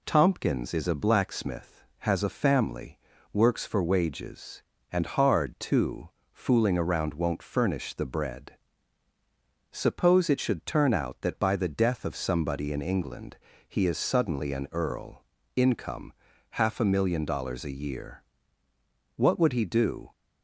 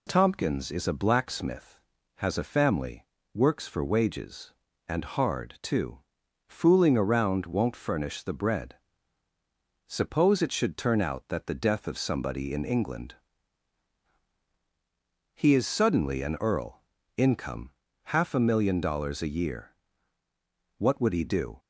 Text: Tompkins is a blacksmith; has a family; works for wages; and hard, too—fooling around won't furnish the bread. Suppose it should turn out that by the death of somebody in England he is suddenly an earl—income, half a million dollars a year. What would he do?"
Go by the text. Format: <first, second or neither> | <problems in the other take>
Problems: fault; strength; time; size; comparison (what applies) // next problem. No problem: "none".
first | skips "by"; at 11.4 s // pauses between "England" and "he"; strong; at 13.1 s; 2.1 s long; slight in the first